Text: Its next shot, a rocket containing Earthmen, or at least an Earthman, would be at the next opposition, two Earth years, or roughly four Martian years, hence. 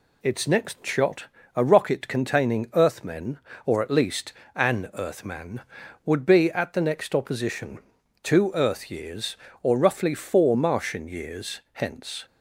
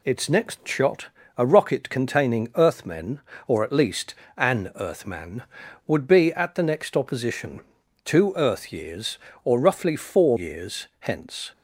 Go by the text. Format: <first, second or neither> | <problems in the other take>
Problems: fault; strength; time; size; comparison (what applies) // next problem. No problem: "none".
first | pauses between "least" and "an"; slight; at 4.1 s; 0.22 s long; slight in the first // skips "Martian"; at 10.3 s